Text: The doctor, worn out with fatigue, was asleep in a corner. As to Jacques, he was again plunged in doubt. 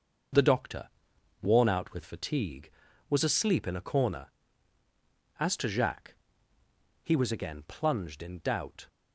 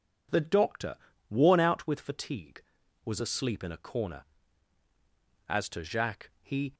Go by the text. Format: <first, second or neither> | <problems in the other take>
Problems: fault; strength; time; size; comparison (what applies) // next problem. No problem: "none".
first | stops before "was again plunged in doubt"; at 6.7 s